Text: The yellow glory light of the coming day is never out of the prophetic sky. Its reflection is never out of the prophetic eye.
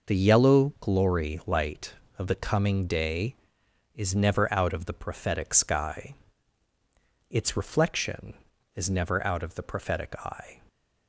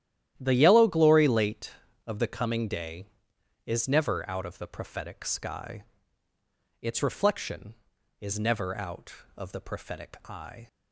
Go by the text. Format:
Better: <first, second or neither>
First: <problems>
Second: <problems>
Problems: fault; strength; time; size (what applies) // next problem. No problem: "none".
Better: first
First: none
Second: starts louder than the rest; strong; until 1.3 s; 11.5 dB // says "late" for "light"; at 1.2 s